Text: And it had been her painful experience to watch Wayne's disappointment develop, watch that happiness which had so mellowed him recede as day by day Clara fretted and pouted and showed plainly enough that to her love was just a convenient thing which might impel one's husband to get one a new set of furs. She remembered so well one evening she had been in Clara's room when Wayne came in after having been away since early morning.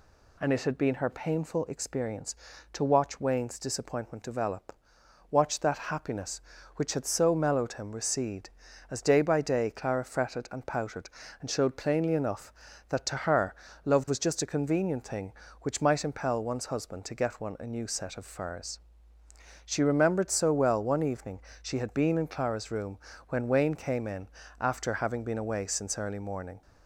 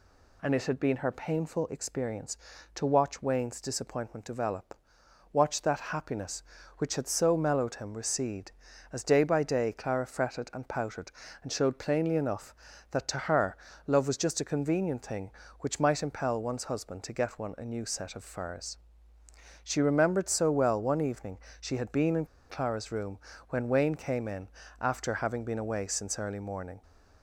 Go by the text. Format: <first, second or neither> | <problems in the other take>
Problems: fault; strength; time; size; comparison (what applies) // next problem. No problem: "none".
first | pauses between "her" and "love"; slight; at 13.5 s; 0.30 s long; slight in the first // pauses between "evening" and "she"; slight; at 21.3 s; 0.22 s long; slight in the first // pauses between "in" and "Clara's"; slight; at 22.2 s; 0.23 s long // pauses between "room" and "when"; slight; at 23.1 s; 0.32 s long; slight in the first // pauses between "in" and "after"; slight; at 24.4 s; 0.32 s long; slight in the first